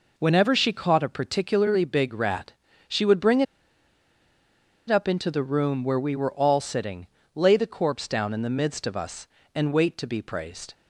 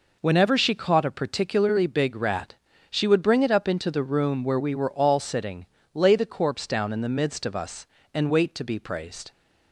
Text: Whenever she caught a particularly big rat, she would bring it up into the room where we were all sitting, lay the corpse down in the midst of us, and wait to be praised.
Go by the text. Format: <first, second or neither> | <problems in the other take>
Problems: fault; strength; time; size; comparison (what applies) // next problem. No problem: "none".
second | pauses between "bring" and "it"; strong; at 3.4 s; 1.4 s long